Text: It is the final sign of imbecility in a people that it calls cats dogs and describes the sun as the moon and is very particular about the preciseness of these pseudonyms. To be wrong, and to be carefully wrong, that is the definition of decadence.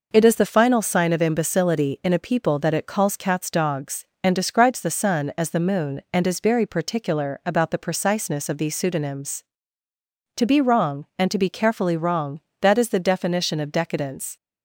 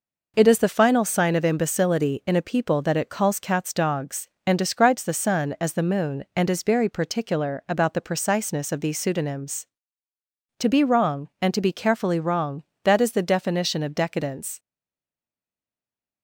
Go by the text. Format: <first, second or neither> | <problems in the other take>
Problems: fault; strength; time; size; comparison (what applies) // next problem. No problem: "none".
first | stays silent after the last word; noticeable; from 14.5 s on; 1.7 s long